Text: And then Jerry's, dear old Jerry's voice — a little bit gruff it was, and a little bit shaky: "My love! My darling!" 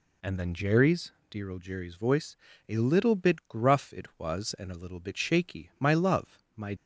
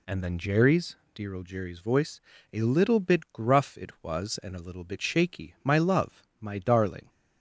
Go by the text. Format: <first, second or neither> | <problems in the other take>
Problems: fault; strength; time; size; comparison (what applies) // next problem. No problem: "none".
second | stops before "darling"; at 6.7 s